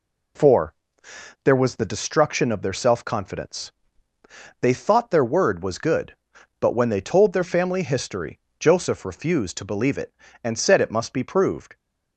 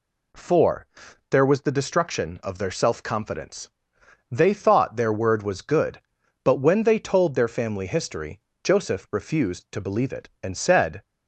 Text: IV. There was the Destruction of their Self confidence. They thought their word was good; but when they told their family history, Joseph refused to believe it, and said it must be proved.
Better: first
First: none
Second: stops before "it must be proved"; at 11.0 s

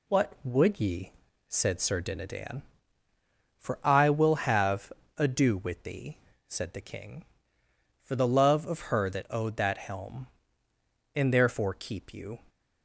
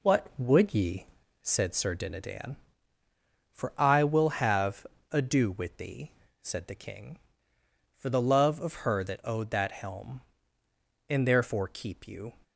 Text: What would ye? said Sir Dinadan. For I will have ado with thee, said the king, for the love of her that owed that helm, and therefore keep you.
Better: first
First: pauses between "have" and "ado"; slight; at 4.9 s; 0.24 s long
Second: starts louder than the rest; slight; until 1.7 s; 3.5 dB // pauses between "have" and "ado"; slight; at 4.8 s; 0.24 s long

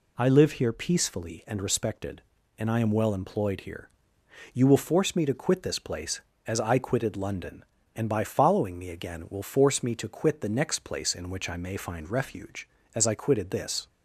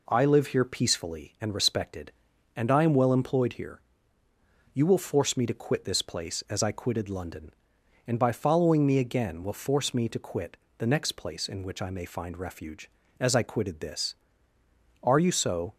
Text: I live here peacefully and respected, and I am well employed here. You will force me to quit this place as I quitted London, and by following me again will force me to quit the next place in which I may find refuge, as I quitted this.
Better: first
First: none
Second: pauses between "quit" and "the"; slight; at 10.5 s; 0.20 s long // goes on to say "Are you so"; noticeable; from 15.0 s on; 0.72 s long

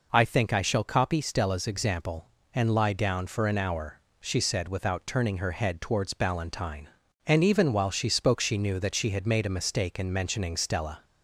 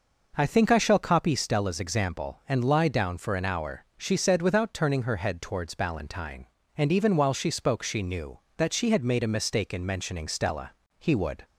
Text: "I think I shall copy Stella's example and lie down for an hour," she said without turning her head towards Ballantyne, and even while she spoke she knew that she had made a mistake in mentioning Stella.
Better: first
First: none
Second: goes on to say "He would"; slight; from 10.9 s on; 0.46 s long

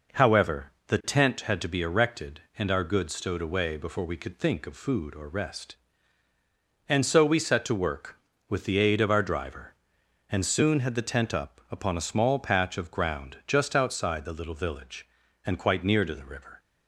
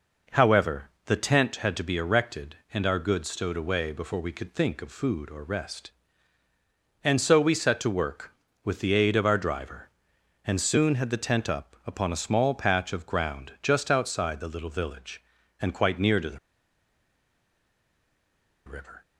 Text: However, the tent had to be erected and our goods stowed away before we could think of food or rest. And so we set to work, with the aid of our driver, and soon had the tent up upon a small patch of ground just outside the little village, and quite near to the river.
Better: first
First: none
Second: pauses between "the" and "river"; strong; at 16.3 s; 2.2 s long

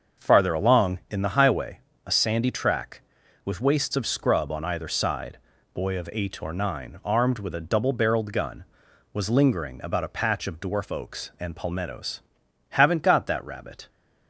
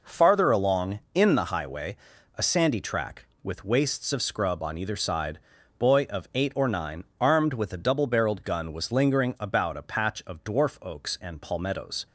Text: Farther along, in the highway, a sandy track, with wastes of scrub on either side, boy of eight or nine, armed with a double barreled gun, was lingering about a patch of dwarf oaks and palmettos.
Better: second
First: starts louder than the rest; until 1.2 s; 6.5 dB // goes on to say "Haven't got that rabbit"; noticeable; from 12.7 s on; 1.1 s long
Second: none

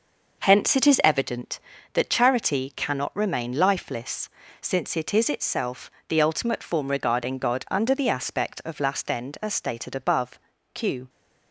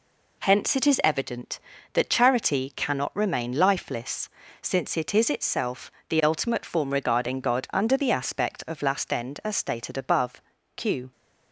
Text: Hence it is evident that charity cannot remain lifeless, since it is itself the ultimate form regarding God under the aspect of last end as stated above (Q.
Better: second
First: starts louder than the rest; noticeable; until 1.6 s; 5.5 dB // pauses between "itself" and "the"; slight; at 5.9 s; 0.16 s long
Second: pauses between "itself" and "the"; slight; at 5.9 s; 0.16 s long

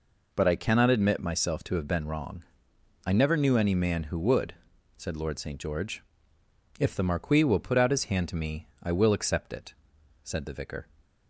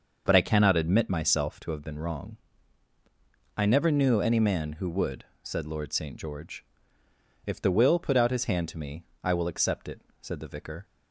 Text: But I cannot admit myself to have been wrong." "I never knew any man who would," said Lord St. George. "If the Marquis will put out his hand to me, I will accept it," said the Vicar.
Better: first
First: none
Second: starts louder than the rest; until 1.2 s; 6 dB // skips "Marquis"; at 7.7 s

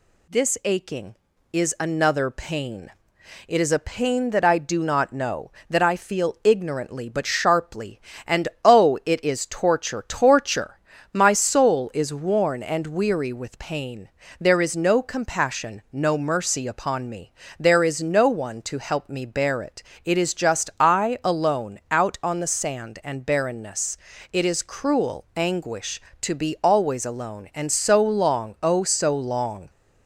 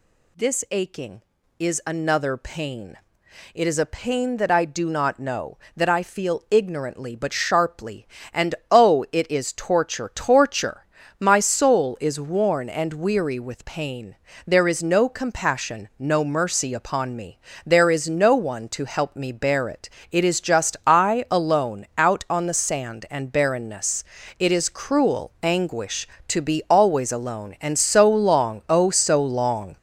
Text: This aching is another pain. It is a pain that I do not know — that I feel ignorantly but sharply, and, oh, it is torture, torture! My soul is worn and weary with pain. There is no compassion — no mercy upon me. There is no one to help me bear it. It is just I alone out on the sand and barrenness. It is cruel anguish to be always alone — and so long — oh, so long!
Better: first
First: none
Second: gets louder; throughout; 6 dB

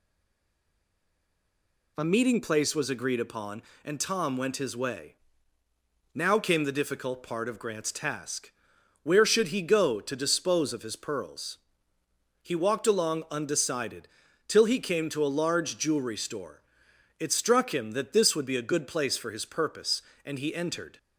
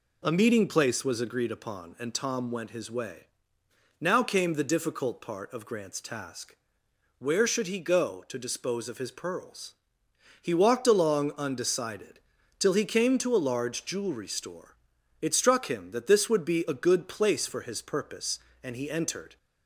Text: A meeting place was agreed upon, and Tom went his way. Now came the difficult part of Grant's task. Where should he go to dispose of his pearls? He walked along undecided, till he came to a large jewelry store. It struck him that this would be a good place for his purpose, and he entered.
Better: second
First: stays silent before the first word; noticeable; until 1.9 s; 1.9 s long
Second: none

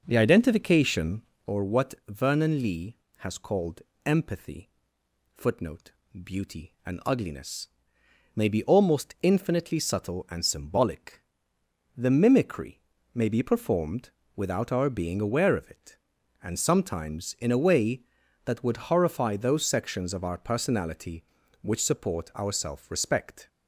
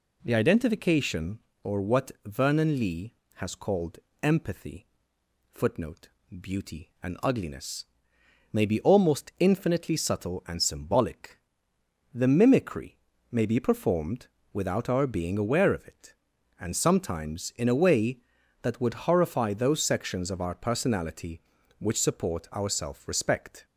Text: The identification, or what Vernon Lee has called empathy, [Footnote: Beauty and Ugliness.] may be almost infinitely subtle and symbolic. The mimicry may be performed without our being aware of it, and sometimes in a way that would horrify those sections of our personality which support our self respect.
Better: second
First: starts louder than the rest; noticeable; until 1.7 s; 5.5 dB // pauses between "what" and "Vernon"; slight; at 1.9 s; 0.16 s long // pauses between "called" and "empathy"; slight; at 3.7 s; 0.24 s long // pauses between "mimicry" and "may"; slight; at 12.8 s; 0.32 s long // pauses between "performed" and "without"; slight; at 14.0 s; 0.26 s long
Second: pauses between "what" and "Vernon"; slight; at 2.1 s; 0.16 s long // pauses between "called" and "empathy"; slight; at 3.9 s; 0.24 s long // pauses between "mimicry" and "may"; slight; at 12.9 s; 0.32 s long // pauses between "performed" and "without"; slight; at 14.2 s; 0.26 s long

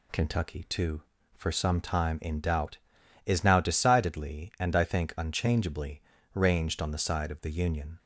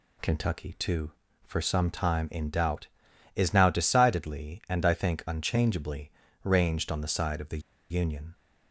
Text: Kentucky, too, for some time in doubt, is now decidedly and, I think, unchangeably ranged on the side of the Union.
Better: first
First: pauses between "unchangeably" and "ranged"; slight; at 6.0 s; 0.34 s long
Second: pauses between "unchangeably" and "ranged"; slight; at 6.0 s; 0.34 s long // pauses between "the" and "Union"; slight; at 7.5 s; 0.30 s long

